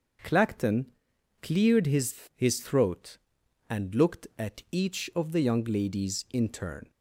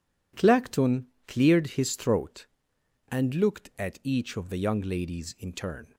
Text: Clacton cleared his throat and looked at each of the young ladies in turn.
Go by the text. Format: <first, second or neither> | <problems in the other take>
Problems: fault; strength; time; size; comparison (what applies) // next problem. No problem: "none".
second | starts louder than the rest; until 1.7 s; 6.5 dB // pauses between "Clacton" and "cleared"; noticeable; at 0.8 s; 0.56 s long; slight in the second // says "his" twice; at 2.3 s